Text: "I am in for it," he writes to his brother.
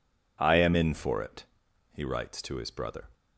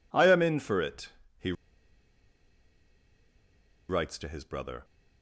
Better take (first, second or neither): first